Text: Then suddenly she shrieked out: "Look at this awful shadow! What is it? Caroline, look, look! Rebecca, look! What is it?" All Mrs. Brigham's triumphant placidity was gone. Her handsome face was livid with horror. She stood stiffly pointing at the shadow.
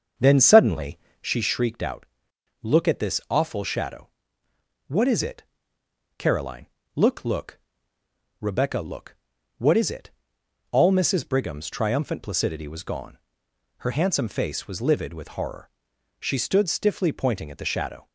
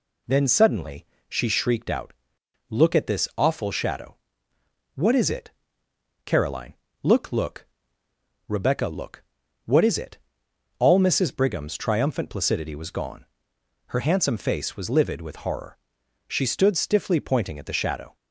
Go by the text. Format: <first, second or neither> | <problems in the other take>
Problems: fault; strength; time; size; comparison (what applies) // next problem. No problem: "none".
second | starts louder than the rest; until 1.3 s; 6.5 dB // pauses between "suddenly" and "she"; slight; at 0.9 s; 0.24 s long; slight in the second